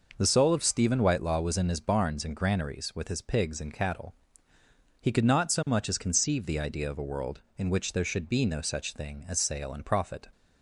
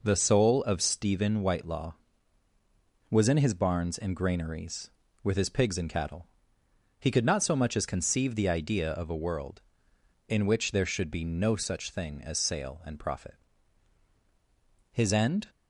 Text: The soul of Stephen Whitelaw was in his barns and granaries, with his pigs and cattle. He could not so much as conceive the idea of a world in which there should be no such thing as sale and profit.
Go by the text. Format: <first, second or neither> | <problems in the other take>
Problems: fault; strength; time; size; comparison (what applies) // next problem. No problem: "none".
first | goes on to say "His end"; from 14.8 s on; 0.60 s long